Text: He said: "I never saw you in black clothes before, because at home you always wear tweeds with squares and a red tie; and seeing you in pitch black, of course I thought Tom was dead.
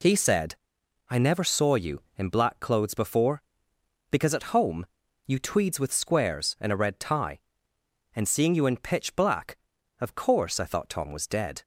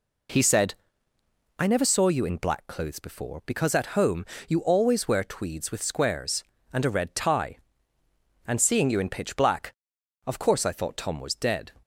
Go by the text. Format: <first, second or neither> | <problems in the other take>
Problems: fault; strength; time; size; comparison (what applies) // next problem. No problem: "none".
second | pauses between "home" and "you"; at 4.8 s; 0.44 s long; slight in the second // skips "always wear"; at 5.3 s